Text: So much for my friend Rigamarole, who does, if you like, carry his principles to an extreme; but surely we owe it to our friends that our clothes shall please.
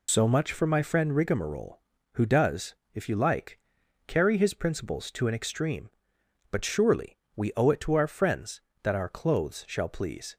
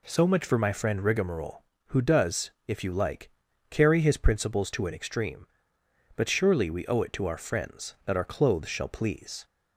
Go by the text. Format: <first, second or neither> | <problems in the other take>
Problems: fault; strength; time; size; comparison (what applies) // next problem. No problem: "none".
second | loses the start of "So"; at 0.0 s; 85 ms // pauses between "surely" and "we"; slight; at 7.1 s; 0.18 s long